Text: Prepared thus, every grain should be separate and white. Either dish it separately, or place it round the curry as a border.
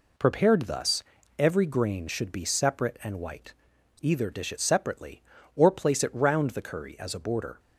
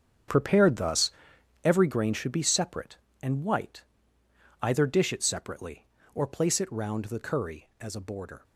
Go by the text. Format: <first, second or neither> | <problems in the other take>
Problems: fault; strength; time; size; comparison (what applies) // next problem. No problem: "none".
first | gets quieter; strong; throughout; 13 dB